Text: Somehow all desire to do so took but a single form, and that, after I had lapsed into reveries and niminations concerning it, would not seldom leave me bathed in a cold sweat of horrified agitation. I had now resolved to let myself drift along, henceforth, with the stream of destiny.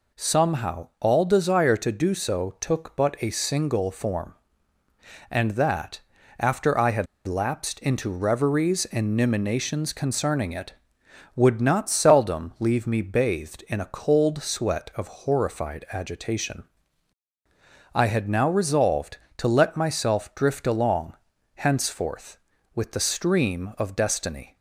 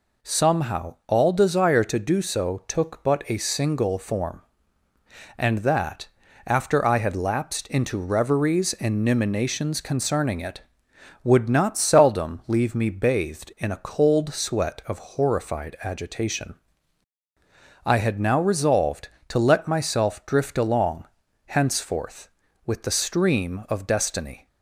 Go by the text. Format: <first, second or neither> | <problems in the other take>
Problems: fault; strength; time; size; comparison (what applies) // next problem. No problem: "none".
second | pauses between "had" and "lapsed"; slight; at 7.0 s; 0.22 s long